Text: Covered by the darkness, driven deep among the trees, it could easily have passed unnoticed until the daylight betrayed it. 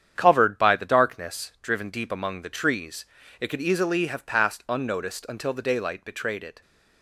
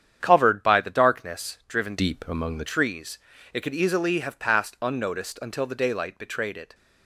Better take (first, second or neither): first